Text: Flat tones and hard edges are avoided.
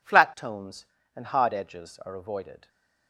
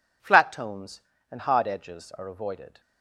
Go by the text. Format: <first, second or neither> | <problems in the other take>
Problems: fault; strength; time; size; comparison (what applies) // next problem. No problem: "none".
neither | none